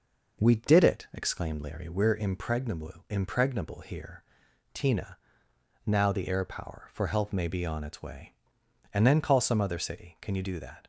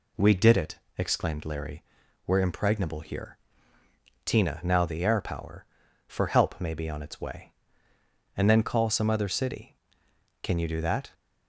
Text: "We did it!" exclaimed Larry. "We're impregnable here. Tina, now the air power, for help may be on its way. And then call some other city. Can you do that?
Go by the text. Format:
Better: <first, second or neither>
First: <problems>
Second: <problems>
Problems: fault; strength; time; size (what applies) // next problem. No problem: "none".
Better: second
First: says "impregnable" twice; at 3.0 s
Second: none